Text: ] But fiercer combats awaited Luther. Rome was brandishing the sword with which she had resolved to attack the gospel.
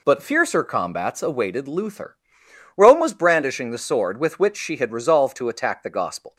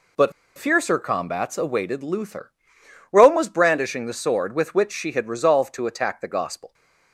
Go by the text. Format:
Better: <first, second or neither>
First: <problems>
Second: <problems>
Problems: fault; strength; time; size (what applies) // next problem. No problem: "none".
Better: first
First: none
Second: pauses between "But" and "fiercer"; slight; at 0.3 s; 0.25 s long